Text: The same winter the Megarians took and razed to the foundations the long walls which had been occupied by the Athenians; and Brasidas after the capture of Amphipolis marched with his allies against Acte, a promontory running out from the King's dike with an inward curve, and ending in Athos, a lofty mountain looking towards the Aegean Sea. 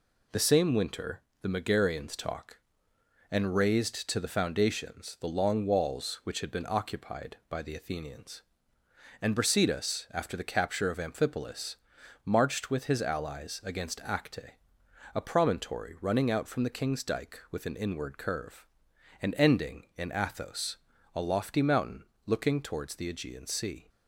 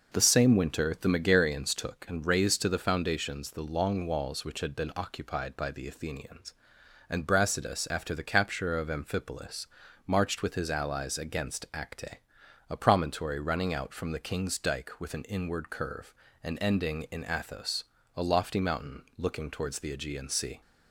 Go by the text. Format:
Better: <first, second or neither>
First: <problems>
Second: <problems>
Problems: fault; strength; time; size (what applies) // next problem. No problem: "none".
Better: second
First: pauses between "winter" and "the"; slight; at 1.2 s; 0.18 s long // says "talk" for "took"; at 2.1 s // pauses between "Amphipolis" and "marched"; noticeable; at 11.7 s; 0.50 s long // pauses between "mountain" and "looking"; slight; at 22.0 s; 0.22 s long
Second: pauses between "Amphipolis" and "marched"; at 9.6 s; 0.40 s long // pauses between "mountain" and "looking"; slight; at 19.0 s; 0.16 s long